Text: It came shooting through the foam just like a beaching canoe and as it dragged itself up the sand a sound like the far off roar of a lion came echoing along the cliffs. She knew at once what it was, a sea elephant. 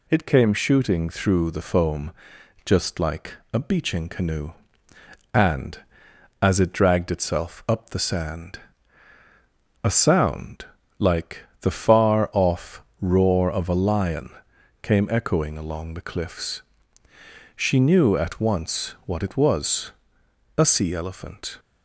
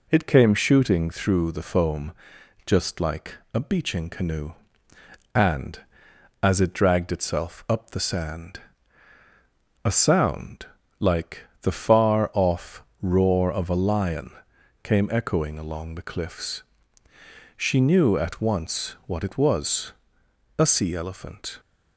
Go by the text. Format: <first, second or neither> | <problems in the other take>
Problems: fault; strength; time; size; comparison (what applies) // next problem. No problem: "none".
first | starts louder than the rest; slight; until 1.2 s; 3 dB // pauses between "foam" and "just"; noticeable; at 2.1 s; 0.54 s long; noticeable in the first // pauses between "like" and "a"; slight; at 3.3 s; 0.18 s long; slight in the first // pauses between "sand" and "a"; at 8.5 s; 1.2 s long; also in the first // pauses between "sound" and "like"; slight; at 10.6 s; 0.34 s long; slight in the first // pauses between "like" and "the"; slight; at 11.4 s; 0.16 s long; slight in the first // pauses between "off" and "roar"; slight; at 12.8 s; 0.18 s long; slight in the first // pauses between "lion" and "came"; noticeable; at 14.2 s; 0.52 s long; noticeable in the first